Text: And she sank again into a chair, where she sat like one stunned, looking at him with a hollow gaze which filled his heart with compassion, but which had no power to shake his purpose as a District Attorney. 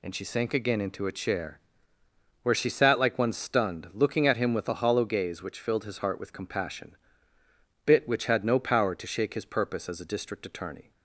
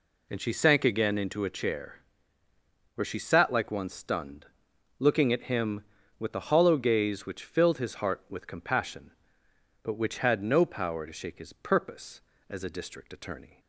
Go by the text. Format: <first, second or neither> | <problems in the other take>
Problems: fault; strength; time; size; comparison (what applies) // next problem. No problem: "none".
second | says "bit" for "but"; at 7.8 s